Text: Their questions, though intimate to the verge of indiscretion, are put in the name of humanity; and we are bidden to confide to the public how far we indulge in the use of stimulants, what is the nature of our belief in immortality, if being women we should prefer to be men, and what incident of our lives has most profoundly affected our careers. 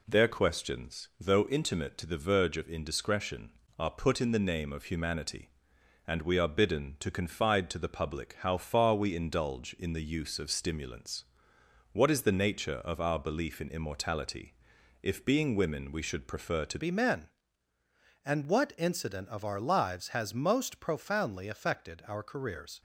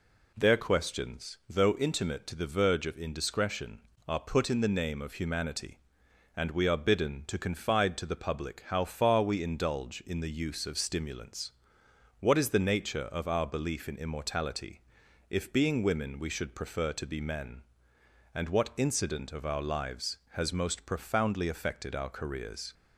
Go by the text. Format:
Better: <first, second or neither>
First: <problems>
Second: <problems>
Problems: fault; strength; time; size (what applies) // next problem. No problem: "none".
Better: second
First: changes voice at "be"; from 16.7 s on; 6.1 s long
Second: none